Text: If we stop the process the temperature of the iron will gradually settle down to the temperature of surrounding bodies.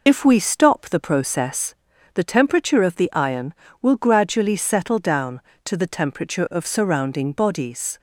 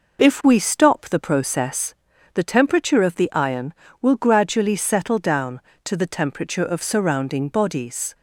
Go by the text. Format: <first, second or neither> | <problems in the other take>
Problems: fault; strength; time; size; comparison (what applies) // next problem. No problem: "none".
second | loses the start of "If"; at 0.0 s; 45 ms // pauses between "process" and "the"; at 1.7 s; 0.40 s long; also in the second